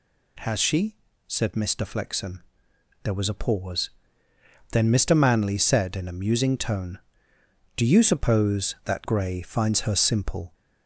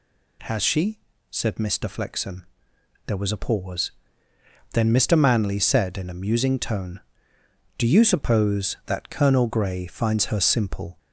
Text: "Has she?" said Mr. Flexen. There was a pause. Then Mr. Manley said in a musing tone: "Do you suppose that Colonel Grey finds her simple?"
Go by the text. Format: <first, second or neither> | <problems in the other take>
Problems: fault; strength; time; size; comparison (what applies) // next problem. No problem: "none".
second | skips "Colonel"; at 9.0 s